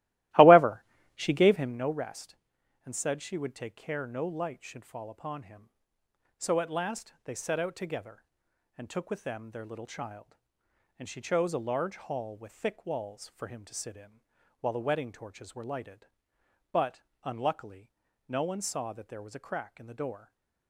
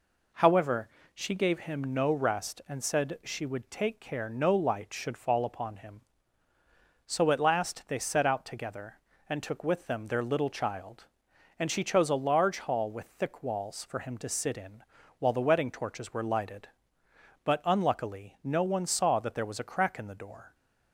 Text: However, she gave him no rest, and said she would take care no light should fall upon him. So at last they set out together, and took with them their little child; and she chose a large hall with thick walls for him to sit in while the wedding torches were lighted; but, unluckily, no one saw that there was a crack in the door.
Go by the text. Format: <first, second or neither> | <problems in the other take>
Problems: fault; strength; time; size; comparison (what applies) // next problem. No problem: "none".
second | starts louder than the rest; strong; until 1.8 s; 16.5 dB // pauses between "in" and "while"; at 14.2 s; 0.40 s long; slight in the second // stays silent after the last word; slight; from 20.1 s on; 0.5 s long